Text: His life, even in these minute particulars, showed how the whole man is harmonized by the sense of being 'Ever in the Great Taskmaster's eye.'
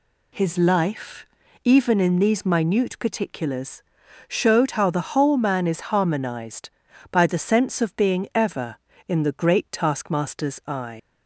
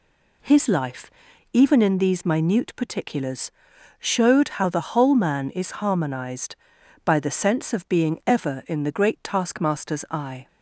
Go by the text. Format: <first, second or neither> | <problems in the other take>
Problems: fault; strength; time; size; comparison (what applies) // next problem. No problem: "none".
second | leaves "eye" unfinished; at 10.9 s; 140 ms